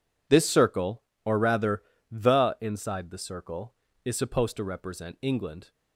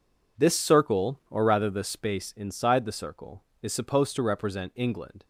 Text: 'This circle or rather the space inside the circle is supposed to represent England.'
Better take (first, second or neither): second